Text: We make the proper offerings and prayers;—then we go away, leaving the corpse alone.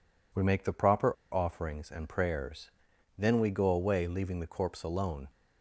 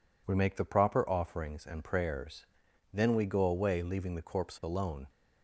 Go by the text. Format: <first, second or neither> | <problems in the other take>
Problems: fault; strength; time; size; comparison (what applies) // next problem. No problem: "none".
second | pauses between "proper" and "offerings"; slight; at 1.1 s; 0.16 s long